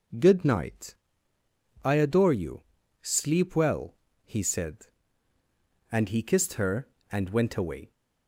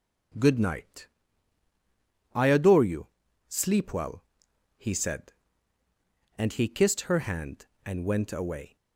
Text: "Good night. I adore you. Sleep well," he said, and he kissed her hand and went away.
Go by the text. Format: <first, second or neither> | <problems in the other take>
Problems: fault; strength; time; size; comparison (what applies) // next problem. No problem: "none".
second | skips "hand"; at 6.9 s